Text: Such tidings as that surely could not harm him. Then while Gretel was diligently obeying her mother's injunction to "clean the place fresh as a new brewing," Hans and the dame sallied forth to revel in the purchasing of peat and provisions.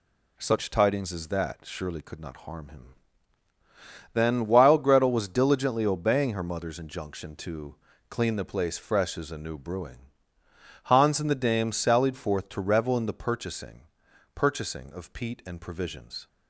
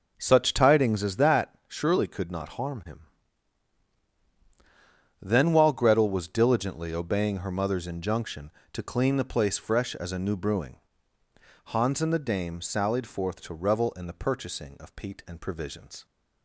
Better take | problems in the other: second | pauses between "to" and "clean"; slight; at 7.7 s; 0.34 s long // says "purchasing" twice; at 14.3 s

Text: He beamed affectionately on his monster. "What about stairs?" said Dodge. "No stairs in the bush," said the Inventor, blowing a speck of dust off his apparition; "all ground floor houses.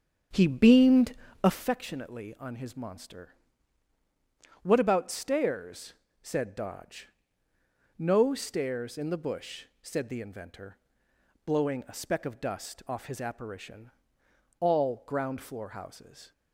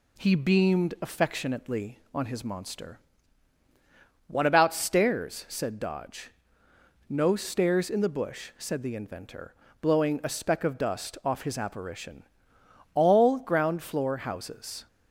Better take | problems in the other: second | starts louder than the rest; strong; until 1.7 s; 7.5 dB // pauses between "beamed" and "affectionately"; slight; at 1.1 s; 0.30 s long

